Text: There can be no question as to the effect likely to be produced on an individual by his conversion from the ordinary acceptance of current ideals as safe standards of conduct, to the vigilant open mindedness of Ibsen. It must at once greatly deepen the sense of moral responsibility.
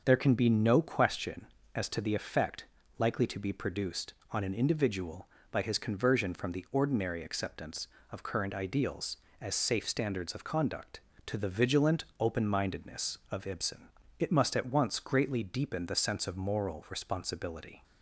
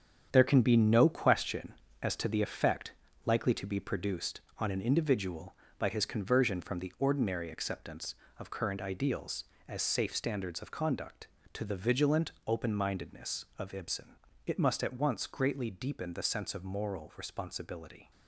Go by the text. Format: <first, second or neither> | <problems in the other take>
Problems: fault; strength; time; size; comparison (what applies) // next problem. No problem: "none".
first | gets quieter; strong; throughout; 8.5 dB // starts louder than the rest; strong; until 1.3 s; 8 dB; also in the first // pauses between "effect" and "likely"; slight; at 2.9 s; 0.32 s long; slight in the first